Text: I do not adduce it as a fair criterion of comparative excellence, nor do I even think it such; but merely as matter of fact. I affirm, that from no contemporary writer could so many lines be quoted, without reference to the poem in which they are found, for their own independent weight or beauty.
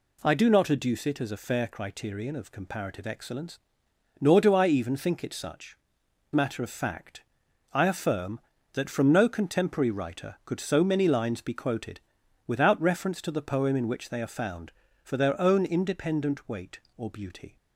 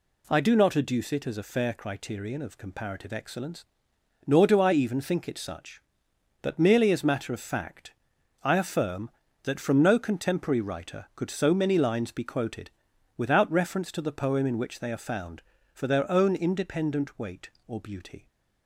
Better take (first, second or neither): second